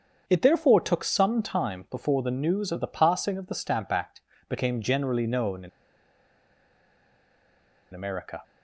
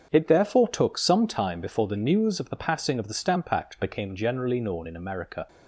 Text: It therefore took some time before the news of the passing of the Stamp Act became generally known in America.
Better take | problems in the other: second | starts louder than the rest; strong; until 1.2 s; 7 dB; also in the second // pauses between "Act" and "became"; slight; at 4.2 s; 0.28 s long // pauses between "in" and "America"; strong; at 5.6 s; 2.2 s long

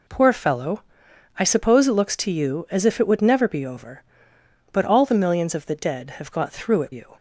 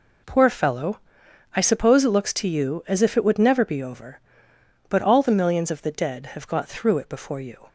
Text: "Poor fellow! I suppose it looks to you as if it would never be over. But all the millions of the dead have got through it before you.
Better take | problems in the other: second | skips "before"; at 6.9 s

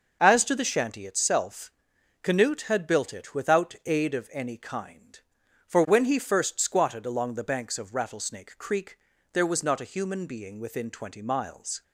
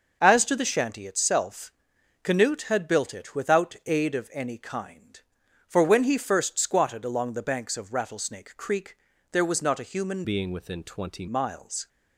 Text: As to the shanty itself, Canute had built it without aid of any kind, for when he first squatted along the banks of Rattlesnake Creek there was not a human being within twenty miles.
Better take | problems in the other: first | starts louder than the rest; noticeable; until 1.2 s; 6 dB // pauses between "Creek" and "there"; slight; at 8.9 s; 0.34 s long; slight in the first // changes voice from "being" to "twenty"; from 10.2 to 11.2 s; 1.0 s long

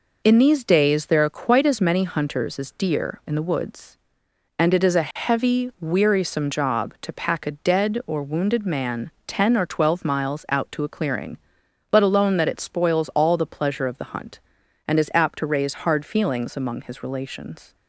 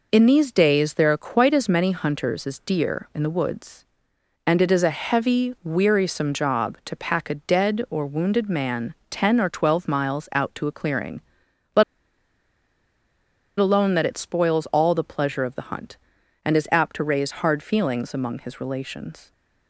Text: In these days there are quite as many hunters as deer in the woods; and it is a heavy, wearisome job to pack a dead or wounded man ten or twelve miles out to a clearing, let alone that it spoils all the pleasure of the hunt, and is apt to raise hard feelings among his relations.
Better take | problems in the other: first | pauses between "man" and "ten"; slight; at 8.9 s; 0.16 s long; slight in the first // pauses between "let" and "alone"; strong; at 11.8 s; 1.7 s long

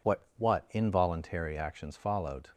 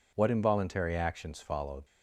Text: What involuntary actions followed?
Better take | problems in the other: second | says "What" twice; at 0.3 s

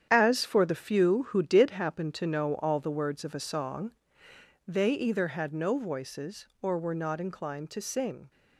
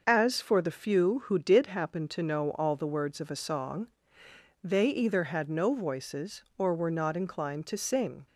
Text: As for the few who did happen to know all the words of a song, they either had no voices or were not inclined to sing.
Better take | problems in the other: second | gets quieter; strong; throughout; 9 dB // starts louder than the rest; strong; until 1.1 s; 9 dB; noticeable in the second

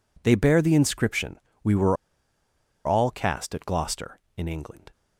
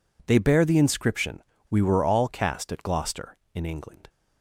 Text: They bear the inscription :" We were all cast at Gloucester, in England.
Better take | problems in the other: second | pauses between "were" and "all"; noticeable; at 1.9 s; 0.89 s long

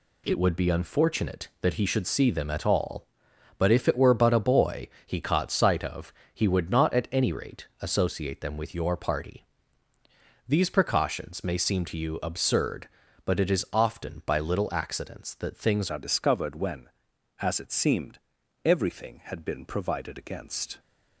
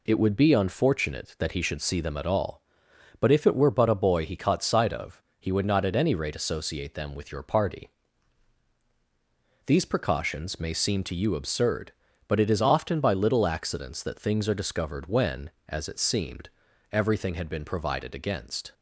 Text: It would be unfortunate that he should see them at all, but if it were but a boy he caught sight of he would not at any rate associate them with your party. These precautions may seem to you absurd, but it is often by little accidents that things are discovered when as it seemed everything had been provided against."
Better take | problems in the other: second | pauses between "boy" and "he"; slight; at 4.8 s; 0.16 s long // pauses between "of" and "he"; slight; at 6.1 s; 0.22 s long; slight in the second // changes voice at "are"; from 15.8 s on; 4.9 s long // pauses between "seemed" and "everything"; at 18.1 s; 0.44 s long; also in the second

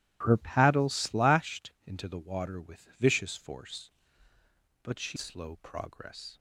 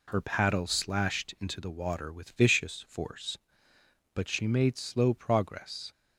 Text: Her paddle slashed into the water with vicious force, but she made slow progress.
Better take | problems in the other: second | pauses between "slashed" and "into"; slight; at 1.7 s; 0.16 s long // skips "made"; at 5.1 s

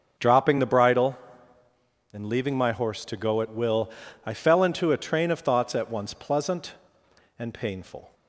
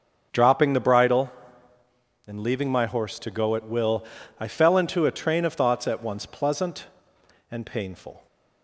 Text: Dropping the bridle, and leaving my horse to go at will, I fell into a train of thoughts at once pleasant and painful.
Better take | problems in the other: neither | starts louder than the rest; the same in both

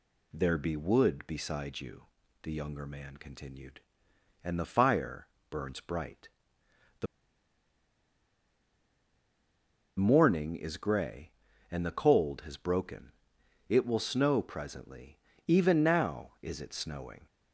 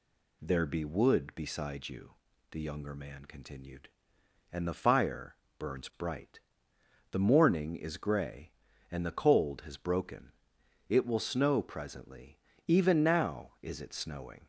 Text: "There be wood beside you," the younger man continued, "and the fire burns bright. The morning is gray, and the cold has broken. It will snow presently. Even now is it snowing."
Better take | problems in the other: second | pauses between "fire" and "burns"; slight; at 5.2 s; 0.22 s long; slight in the second // pauses between "The" and "morning"; strong; at 7.0 s; 2.9 s long

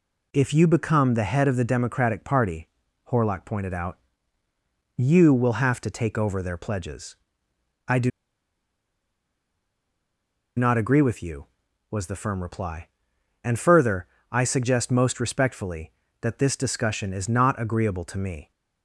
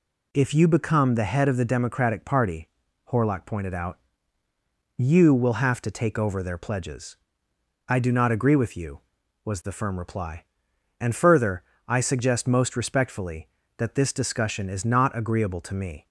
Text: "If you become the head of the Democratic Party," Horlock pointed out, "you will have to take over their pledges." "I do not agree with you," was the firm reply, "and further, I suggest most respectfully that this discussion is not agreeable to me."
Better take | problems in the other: second | pauses between "do" and "not"; strong; at 8.1 s; 2.4 s long

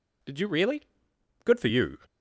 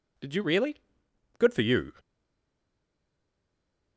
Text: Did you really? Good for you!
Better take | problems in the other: first | stays silent after the last word; noticeable; from 1.9 s on; 2.0 s long

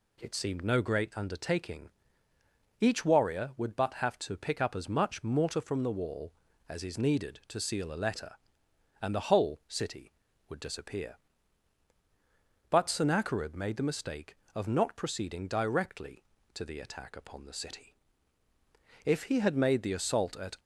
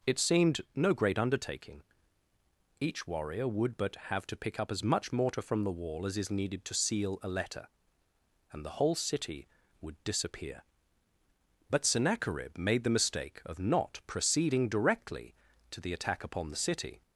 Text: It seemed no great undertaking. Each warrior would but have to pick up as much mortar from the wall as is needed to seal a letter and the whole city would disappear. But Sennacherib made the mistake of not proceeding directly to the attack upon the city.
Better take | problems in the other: second | goes on to say "If he had made the assault at"; from 19.0 s on; 1.5 s long

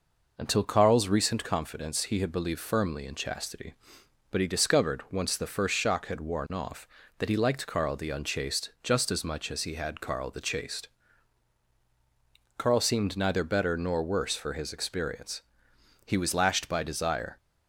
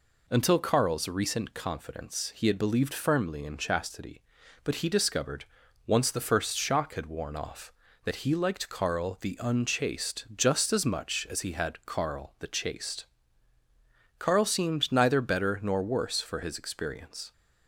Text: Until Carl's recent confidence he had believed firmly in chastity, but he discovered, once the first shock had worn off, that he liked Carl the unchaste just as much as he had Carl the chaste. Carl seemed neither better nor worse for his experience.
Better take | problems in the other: second | goes on to say "He was lashed by desire"; from 16.0 s on; 1.3 s long

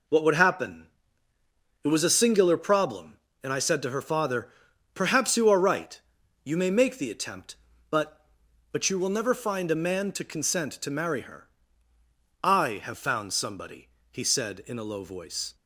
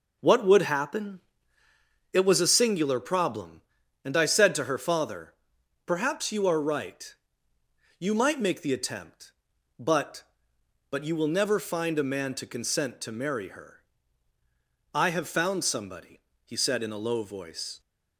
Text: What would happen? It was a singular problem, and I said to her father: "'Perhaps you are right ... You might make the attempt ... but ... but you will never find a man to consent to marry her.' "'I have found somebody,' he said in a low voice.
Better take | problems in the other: second | says "may" for "might"; at 6.5 s

